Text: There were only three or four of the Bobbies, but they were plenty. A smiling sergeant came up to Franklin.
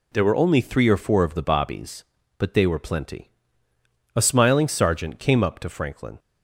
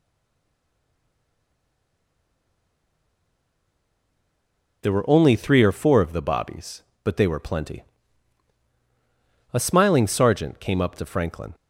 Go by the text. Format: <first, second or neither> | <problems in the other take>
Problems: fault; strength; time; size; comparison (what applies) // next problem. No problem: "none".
first | stays silent before the first word; strong; until 4.8 s; 4.8 s long